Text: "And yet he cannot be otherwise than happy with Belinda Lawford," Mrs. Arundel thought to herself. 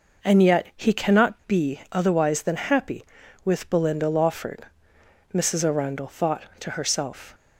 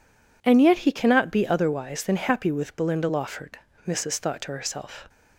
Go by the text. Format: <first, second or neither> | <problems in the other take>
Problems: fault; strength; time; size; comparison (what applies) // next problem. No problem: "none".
first | skips "Arundel"; at 4.1 s